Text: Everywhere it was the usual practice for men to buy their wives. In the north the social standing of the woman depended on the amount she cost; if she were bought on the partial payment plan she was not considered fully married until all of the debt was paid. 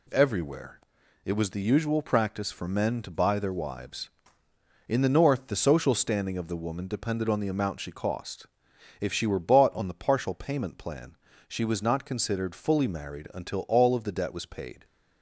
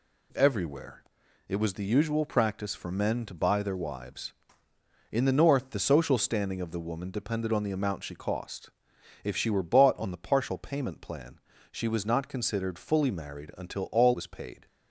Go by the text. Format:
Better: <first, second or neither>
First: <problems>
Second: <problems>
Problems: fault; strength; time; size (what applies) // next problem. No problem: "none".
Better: first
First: pauses between "Everywhere" and "it"; noticeable; at 0.7 s; 0.46 s long // pauses between "plan" and "she"; slight; at 11.1 s; 0.28 s long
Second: pauses between "Everywhere" and "it"; noticeable; at 1.0 s; 0.46 s long // pauses between "plan" and "she"; slight; at 11.4 s; 0.28 s long // skips "of the debt"; at 14.1 s